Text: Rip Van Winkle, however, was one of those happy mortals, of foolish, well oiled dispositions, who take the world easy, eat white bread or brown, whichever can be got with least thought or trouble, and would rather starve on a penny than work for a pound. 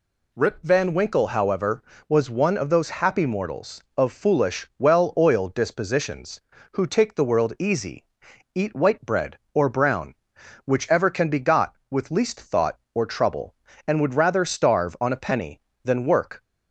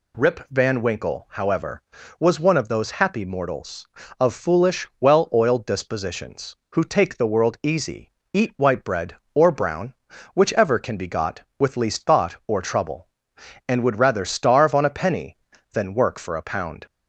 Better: second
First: stops before "for a pound"; at 16.4 s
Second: none

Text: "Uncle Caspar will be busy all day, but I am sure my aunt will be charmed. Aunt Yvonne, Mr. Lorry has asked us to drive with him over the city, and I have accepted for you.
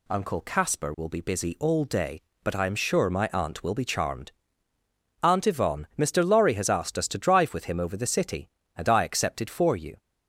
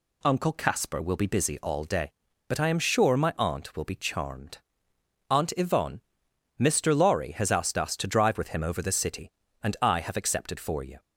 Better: second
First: skips "have"; at 9.0 s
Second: none

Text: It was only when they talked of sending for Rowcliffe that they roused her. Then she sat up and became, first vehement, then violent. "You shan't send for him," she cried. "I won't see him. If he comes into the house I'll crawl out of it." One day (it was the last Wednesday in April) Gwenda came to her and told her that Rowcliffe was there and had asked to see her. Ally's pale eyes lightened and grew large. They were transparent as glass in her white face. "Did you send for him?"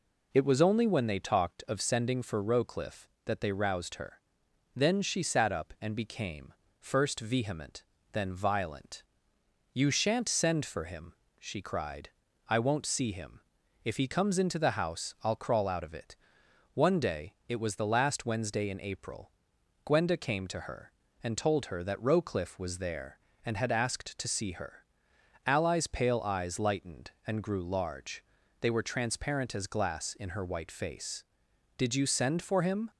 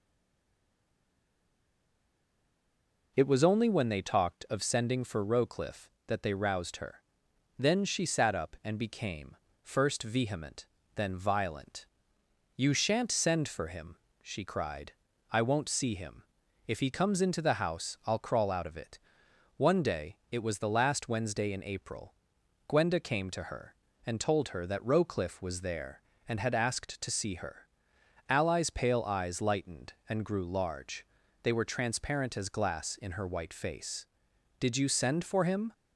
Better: first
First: none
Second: stays silent before the first word; strong; until 3.1 s; 3.1 s long

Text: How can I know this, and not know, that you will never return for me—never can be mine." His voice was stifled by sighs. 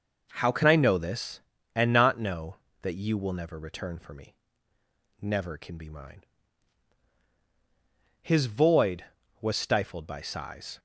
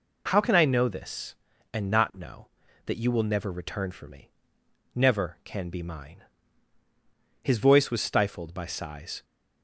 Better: second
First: says "void" for "voice"; at 8.4 s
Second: none

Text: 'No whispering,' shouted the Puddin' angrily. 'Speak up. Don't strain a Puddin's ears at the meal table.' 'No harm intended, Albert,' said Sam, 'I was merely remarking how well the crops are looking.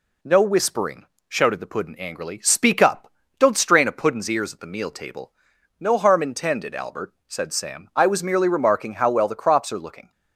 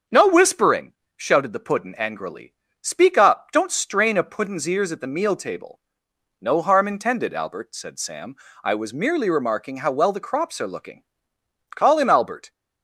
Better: first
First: none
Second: starts louder than the rest; until 1.3 s; 7 dB // goes on to say "Call him Albert"; noticeable; from 11.7 s on; 0.76 s long

